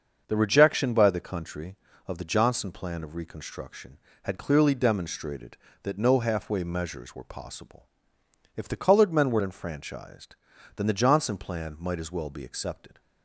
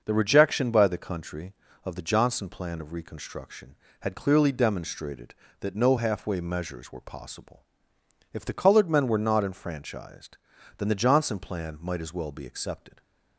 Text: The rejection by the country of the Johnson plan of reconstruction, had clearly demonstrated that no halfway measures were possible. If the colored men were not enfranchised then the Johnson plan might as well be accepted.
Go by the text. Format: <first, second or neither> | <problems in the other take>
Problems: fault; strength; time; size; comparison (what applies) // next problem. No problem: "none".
second | starts louder than the rest; until 1.2 s; 6.5 dB; noticeable in the second // skips "not"; at 9.4 s // pauses between "enfranchised" and "then"; at 10.3 s; 0.40 s long; also in the second